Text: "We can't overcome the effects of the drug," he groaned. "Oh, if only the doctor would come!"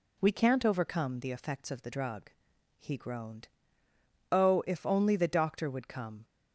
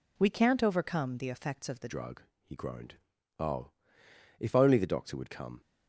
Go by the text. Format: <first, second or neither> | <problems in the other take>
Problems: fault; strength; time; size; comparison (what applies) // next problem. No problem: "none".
first | changes voice at "drug"; from 1.8 s on; 3.8 s long